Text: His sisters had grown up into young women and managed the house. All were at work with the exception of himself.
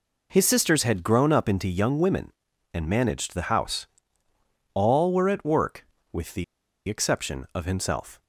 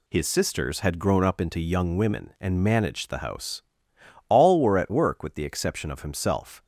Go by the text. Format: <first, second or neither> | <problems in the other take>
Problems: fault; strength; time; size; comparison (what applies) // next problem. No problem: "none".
second | pauses between "the" and "exception"; at 6.4 s; 0.44 s long